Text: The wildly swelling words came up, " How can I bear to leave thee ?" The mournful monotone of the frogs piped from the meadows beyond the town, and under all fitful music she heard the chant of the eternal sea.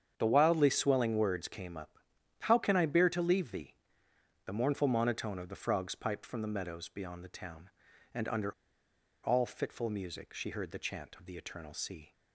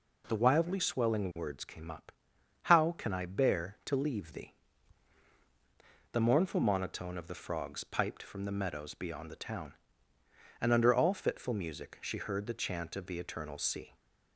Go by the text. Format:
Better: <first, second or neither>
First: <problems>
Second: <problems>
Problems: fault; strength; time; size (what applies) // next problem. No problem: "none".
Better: second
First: starts louder than the rest; strong; until 1.1 s; 8 dB // pauses between "under" and "all"; noticeable; at 8.5 s; 0.70 s long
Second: starts louder than the rest; noticeable; until 1.2 s; 6 dB